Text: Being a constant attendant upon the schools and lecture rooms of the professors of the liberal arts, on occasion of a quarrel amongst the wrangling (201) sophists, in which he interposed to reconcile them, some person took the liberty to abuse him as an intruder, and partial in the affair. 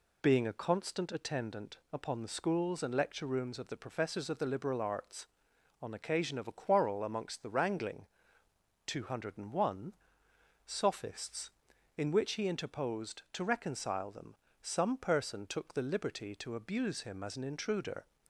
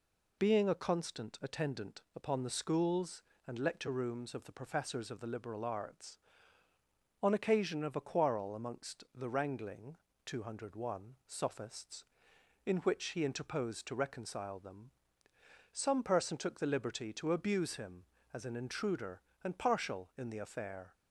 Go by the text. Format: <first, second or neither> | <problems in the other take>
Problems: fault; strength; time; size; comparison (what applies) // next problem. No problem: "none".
second | stops before "and partial in the affair"; at 18.2 s